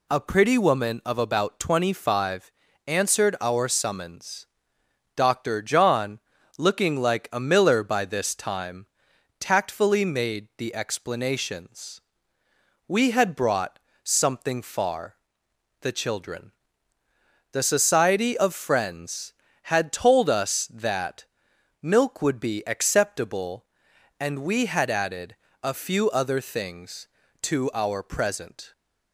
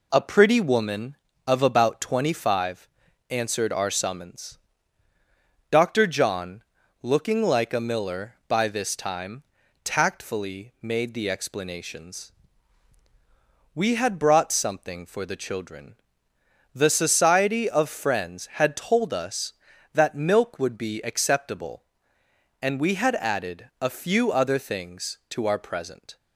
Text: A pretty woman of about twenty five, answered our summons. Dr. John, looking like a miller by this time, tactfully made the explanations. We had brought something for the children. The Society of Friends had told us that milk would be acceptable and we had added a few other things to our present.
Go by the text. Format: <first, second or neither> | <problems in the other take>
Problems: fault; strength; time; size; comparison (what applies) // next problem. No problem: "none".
second | pauses between "brought" and "something"; slight; at 13.7 s; 0.22 s long // says "far" for "for"; at 14.6 s // pauses between "that" and "milk"; noticeable; at 21.2 s; 0.56 s long // pauses between "added" and "a"; slight; at 25.3 s; 0.26 s long